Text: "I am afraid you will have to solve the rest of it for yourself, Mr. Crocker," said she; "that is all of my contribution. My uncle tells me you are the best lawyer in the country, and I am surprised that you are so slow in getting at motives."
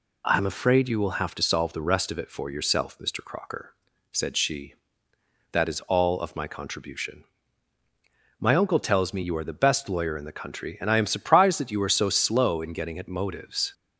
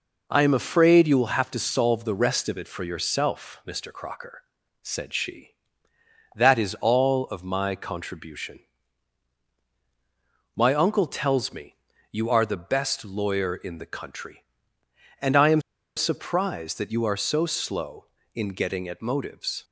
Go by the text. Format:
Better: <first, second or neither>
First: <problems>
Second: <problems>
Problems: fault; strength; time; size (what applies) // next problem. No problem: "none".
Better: first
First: none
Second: pauses between "me" and "you"; slight; at 11.7 s; 0.36 s long // pauses between "am" and "surprised"; slight; at 15.6 s; 0.35 s long